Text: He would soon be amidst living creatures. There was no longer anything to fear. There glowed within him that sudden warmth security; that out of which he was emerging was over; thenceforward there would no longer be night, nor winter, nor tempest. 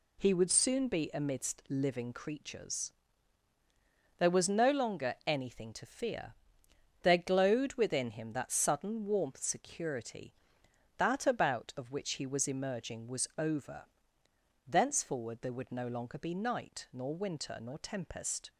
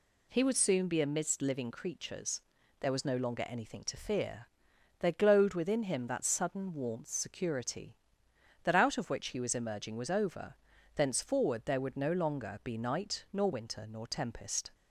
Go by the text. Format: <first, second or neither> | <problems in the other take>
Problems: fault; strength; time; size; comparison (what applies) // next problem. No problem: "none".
second | says "about" for "out"; at 11.2 s